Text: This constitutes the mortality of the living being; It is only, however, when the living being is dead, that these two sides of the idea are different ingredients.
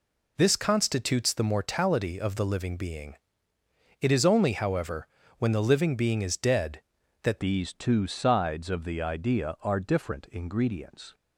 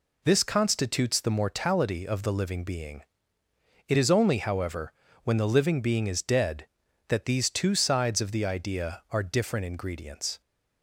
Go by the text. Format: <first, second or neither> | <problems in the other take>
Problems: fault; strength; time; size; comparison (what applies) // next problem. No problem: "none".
second | changes voice at "these"; from 7.3 s on; 3.8 s long